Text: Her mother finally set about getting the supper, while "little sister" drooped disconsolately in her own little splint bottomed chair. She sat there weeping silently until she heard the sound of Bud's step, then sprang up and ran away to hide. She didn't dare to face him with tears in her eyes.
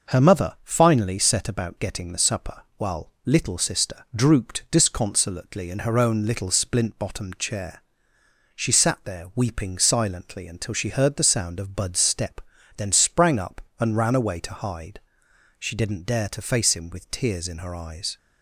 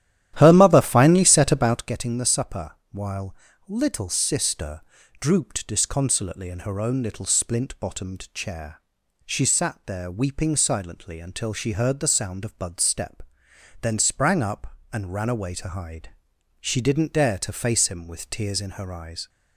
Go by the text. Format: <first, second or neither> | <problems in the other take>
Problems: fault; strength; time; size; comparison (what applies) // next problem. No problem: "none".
first | starts louder than the rest; strong; until 1.9 s; 12 dB // pauses between "while" and "little"; slight; at 3.3 s; 0.32 s long // pauses between "sister" and "drooped"; at 4.8 s; 0.40 s long